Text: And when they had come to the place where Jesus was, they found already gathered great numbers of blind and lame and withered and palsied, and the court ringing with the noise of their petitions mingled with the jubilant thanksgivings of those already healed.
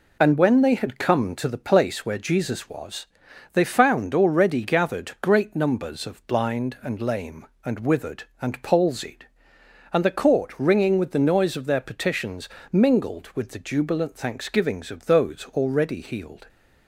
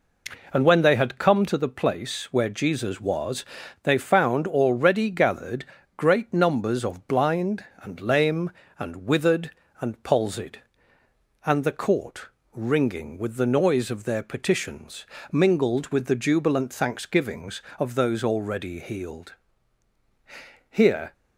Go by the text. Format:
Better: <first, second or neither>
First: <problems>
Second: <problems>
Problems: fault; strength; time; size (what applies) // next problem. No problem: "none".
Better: first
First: pauses between "petitions" and "mingled"; slight; at 12.4 s; 0.24 s long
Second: pauses between "gathered" and "great"; slight; at 5.6 s; 0.32 s long // pauses between "court" and "ringing"; slight; at 12.2 s; 0.26 s long // pauses between "petitions" and "mingled"; slight; at 15.0 s; 0.26 s long // goes on to say "Here"; slight; from 20.6 s on; 0.44 s long